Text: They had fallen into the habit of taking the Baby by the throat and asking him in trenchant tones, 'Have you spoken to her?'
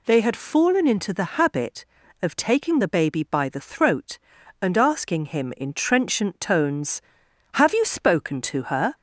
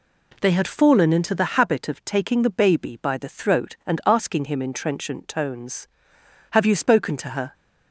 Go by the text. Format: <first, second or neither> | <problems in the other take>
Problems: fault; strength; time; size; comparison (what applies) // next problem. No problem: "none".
neither | none